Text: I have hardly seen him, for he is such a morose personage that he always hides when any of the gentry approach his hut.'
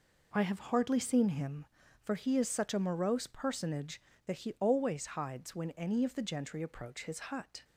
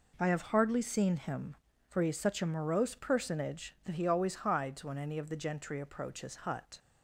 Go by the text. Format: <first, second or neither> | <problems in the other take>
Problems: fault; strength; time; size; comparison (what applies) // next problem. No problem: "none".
neither | none